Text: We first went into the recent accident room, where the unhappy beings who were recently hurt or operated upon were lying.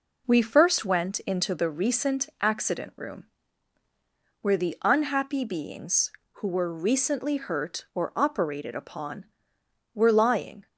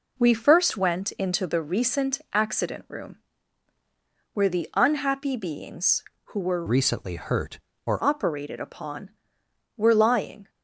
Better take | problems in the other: first | changes voice from "recently" to "or"; from 6.6 to 8.0 s; 1.4 s long

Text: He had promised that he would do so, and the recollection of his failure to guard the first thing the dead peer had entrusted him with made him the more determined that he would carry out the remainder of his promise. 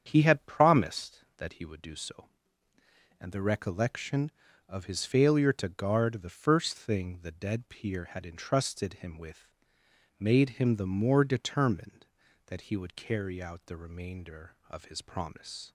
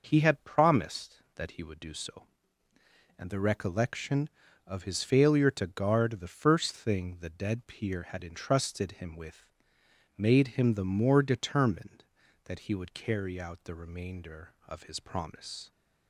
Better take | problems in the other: second | starts louder than the rest; strong; until 1.3 s; 8 dB // pauses between "with" and "made"; noticeable; at 9.5 s; 0.66 s long; noticeable in the second

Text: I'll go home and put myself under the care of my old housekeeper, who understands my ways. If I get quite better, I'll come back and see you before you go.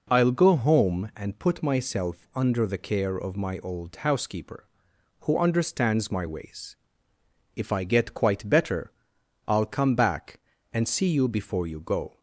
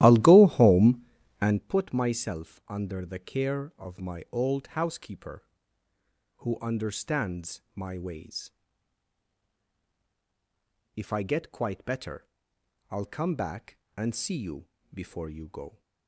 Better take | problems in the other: first | starts louder than the rest; strong; until 1.6 s; 14 dB // pauses between "you" and "before"; slight; at 14.6 s; 0.26 s long

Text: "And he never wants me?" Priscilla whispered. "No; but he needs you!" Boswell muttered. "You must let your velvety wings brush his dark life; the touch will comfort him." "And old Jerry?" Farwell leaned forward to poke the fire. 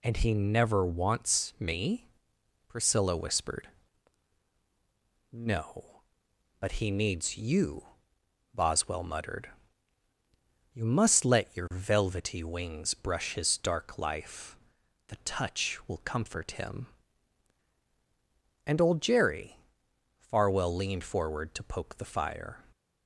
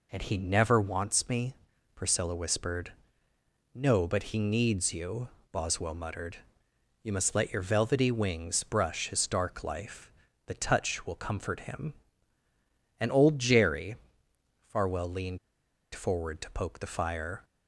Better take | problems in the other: first | pauses between "leaned" and "forward"; noticeable; at 15.3 s; 0.55 s long

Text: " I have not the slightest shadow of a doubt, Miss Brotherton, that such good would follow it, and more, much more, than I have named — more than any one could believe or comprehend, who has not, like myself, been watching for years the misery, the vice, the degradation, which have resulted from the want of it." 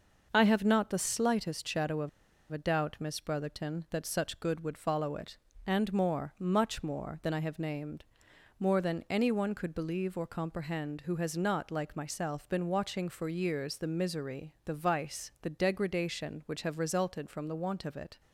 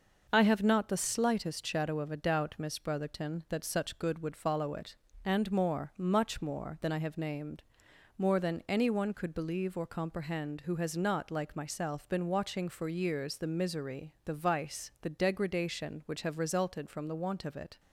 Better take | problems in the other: second | pauses between "of" and "a"; at 2.0 s; 0.42 s long

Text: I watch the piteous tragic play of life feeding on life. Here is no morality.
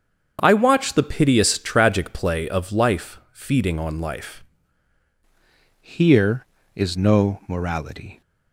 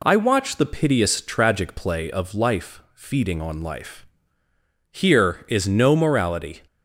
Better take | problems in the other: second | starts louder than the rest; until 1.4 s; 7 dB // changes voice at "Here"; from 5.8 s on; 2.4 s long

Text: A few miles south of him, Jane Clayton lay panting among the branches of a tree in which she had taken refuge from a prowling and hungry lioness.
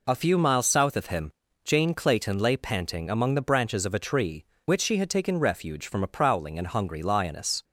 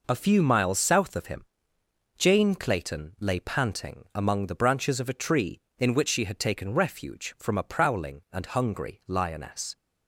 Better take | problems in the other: second | skips "in"; at 4.5 s

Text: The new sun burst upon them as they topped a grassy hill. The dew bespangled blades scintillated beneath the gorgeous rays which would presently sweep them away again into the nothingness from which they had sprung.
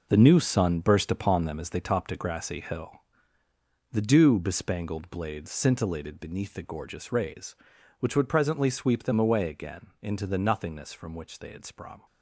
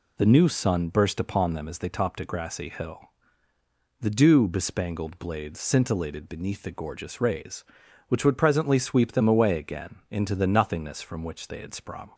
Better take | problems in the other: second | gets quieter; strong; throughout; 9.5 dB

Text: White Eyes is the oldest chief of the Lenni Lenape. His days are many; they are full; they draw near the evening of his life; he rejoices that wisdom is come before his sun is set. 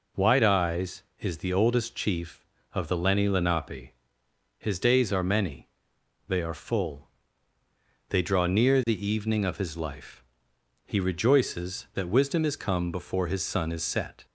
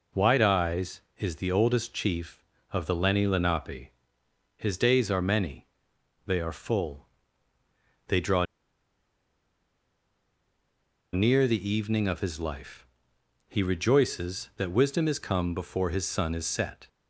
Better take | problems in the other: first | pauses between "draw" and "near"; strong; at 8.4 s; 2.6 s long

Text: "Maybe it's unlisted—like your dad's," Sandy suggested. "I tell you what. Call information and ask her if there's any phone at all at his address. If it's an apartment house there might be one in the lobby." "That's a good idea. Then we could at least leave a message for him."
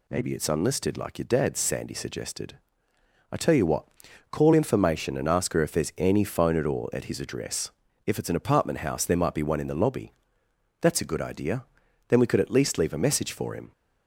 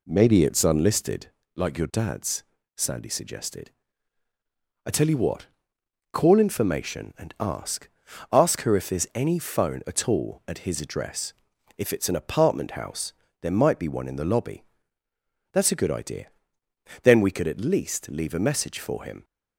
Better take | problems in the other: first | says "ask" twice; at 8.3 s // pauses between "house" and "there"; slight; at 13.1 s; 0.26 s long

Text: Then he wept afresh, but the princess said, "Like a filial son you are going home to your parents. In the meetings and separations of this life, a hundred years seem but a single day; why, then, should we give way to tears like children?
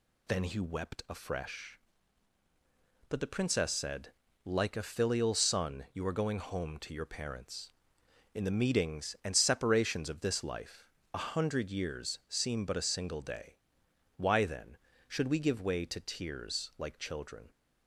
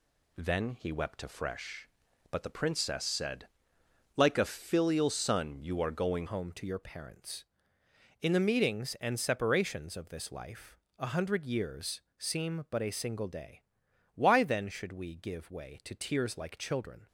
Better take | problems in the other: first | changes voice at "home"; from 6.2 s on; 10.8 s long // pauses between "years" and "seem"; slight; at 12.0 s; 0.16 s long

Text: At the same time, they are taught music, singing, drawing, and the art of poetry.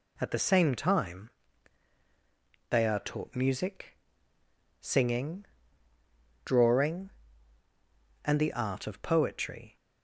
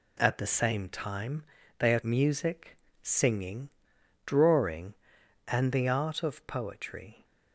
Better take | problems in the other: first | skips "taught"; at 2.0 s

